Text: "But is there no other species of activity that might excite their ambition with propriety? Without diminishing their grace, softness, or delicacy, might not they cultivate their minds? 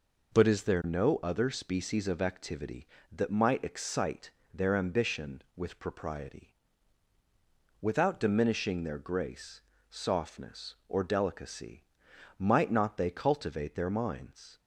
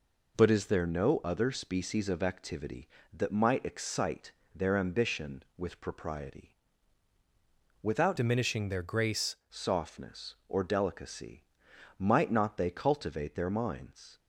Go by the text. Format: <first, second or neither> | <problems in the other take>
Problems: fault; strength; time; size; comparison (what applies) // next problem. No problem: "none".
first | pauses between "excite" and "their"; slight; at 4.3 s; 0.22 s long; slight in the first // changes voice from "diminishing" to "grace"; from 8.1 to 9.3 s; 1.2 s long